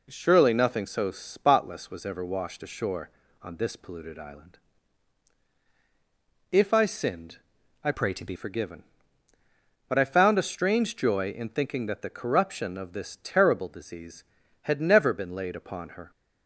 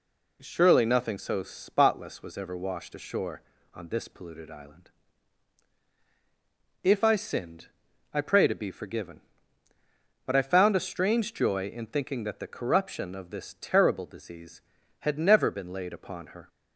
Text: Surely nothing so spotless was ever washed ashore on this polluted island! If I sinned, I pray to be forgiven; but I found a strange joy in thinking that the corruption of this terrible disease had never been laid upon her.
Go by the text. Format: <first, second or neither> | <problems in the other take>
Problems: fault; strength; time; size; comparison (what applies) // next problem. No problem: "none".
second | changes voice from "pray" to "be"; from 7.9 to 8.3 s; 0.4 s long